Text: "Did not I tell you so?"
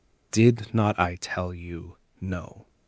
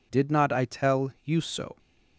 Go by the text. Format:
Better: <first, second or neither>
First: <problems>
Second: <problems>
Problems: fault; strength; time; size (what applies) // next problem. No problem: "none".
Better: second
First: says "no" for "so"; at 2.2 s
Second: none